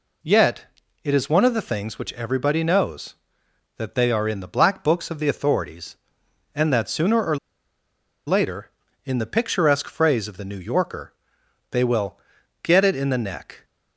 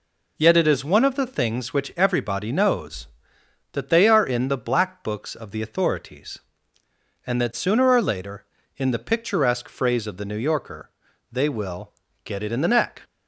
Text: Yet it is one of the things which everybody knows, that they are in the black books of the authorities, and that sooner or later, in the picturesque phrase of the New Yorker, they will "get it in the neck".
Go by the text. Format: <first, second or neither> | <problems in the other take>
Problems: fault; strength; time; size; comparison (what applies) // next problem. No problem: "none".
second | pauses between "Yet" and "it"; slight; at 0.6 s; 0.36 s long // pauses between "or" and "later"; noticeable; at 7.3 s; 0.90 s long // pauses between "will" and "get"; at 12.1 s; 0.44 s long; slight in the second